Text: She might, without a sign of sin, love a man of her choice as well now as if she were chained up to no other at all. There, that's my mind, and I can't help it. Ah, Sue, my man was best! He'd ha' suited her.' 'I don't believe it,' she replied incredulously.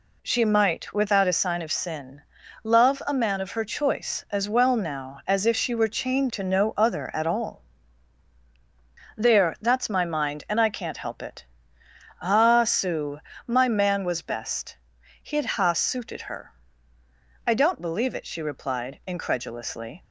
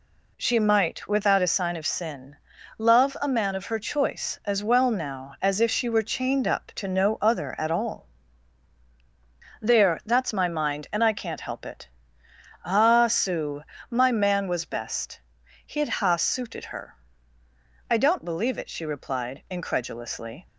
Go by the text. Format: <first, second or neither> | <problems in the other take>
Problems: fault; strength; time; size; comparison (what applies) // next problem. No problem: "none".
second | skips "up"; at 6.2 s